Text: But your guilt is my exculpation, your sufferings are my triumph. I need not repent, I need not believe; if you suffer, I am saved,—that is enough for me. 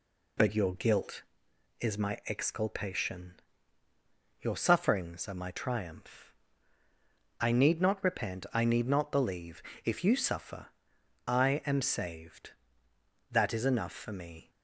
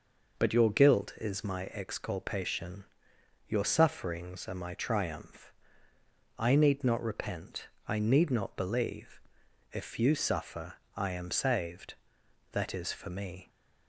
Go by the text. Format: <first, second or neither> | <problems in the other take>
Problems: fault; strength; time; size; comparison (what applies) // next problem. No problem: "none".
first | skips "enough"; at 12.9 s